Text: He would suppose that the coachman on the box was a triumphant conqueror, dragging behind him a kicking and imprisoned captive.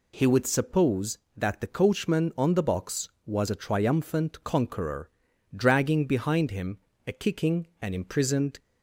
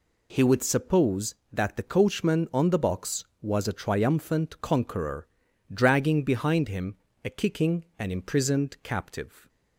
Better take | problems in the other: second | pauses between "him" and "a"; slight; at 6.7 s; 0.30 s long; slight in the second // stops before "captive"; at 8.5 s

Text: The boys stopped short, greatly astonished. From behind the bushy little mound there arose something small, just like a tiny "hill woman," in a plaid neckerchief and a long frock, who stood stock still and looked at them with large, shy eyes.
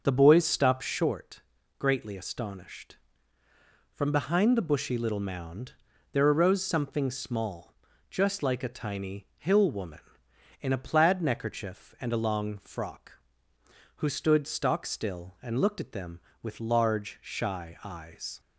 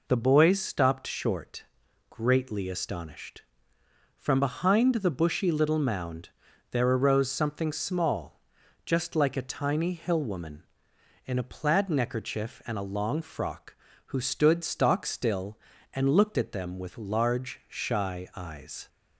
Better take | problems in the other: second | starts louder than the rest; until 1.2 s; 6 dB // pauses between "mound" and "there"; at 5.7 s; 0.38 s long; also in the second

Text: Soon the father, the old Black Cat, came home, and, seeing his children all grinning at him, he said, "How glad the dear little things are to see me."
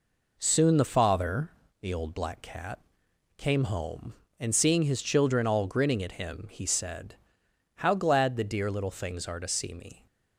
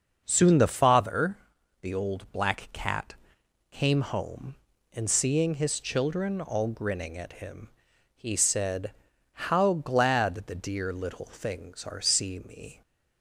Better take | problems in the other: first | starts louder than the rest; until 1.2 s; 6 dB // skips "to"; at 12.0 s

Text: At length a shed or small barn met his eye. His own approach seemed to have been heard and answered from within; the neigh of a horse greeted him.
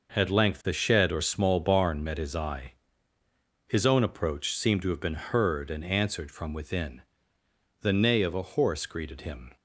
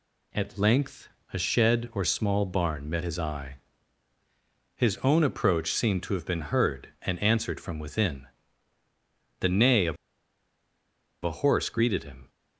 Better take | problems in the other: first | pauses between "length" and "a"; slight; at 1.0 s; 0.24 s long // pauses between "of" and "a"; strong; at 9.9 s; 1.2 s long

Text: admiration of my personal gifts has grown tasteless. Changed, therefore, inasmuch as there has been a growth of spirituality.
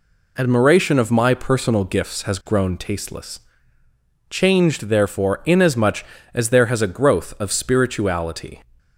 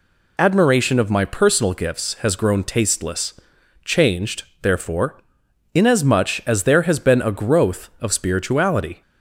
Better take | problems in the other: second | skips "been"; at 6.8 s

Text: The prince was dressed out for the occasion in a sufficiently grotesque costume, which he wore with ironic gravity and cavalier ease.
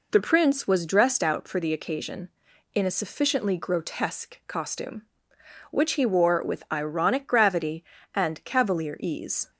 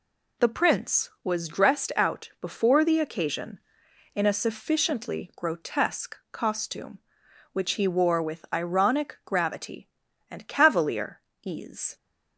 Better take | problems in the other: first | says "before" for "for"; at 2.4 s // pauses between "cavalier" and "ease"; slight; at 11.2 s; 0.20 s long

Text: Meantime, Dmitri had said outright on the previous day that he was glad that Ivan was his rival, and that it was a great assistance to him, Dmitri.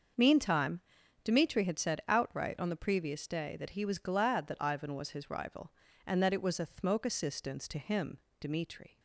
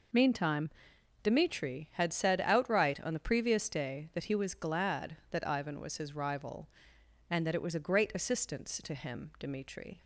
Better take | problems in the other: second | starts louder than the rest; until 1.5 s; 6.5 dB // says "thmoke" for "great"; at 6.6 s

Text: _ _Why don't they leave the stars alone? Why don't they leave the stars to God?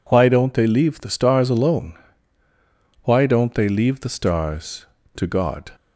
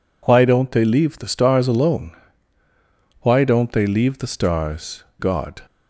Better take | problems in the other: first | skips "to"; at 5.1 s

